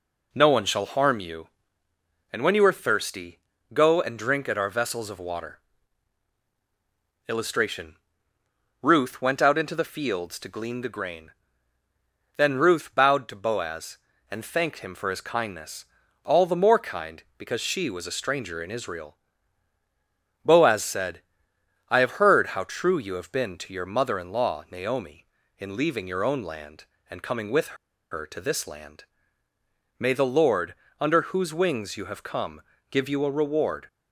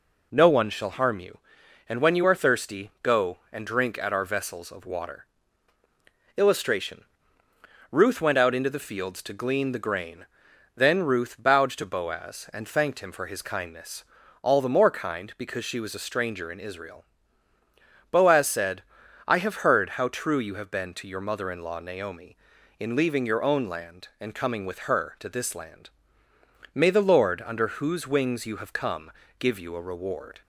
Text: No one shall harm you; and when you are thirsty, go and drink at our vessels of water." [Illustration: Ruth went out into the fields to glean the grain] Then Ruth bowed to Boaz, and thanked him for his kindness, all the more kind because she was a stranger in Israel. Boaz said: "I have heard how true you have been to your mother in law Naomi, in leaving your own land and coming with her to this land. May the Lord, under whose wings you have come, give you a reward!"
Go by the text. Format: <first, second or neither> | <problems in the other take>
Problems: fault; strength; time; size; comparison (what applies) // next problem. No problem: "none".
second | pauses between "grain" and "Then"; at 11.3 s; 1.0 s long; noticeable in the second // pauses between "with" and "her"; at 27.7 s; 0.36 s long